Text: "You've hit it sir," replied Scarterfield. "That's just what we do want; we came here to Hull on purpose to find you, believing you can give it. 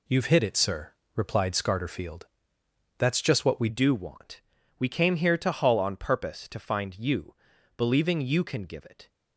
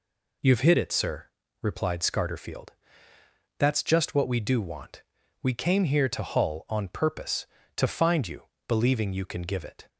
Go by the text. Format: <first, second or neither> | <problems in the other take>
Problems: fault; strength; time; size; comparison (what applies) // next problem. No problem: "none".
second | changes voice at "do"; from 3.6 s on; 5.4 s long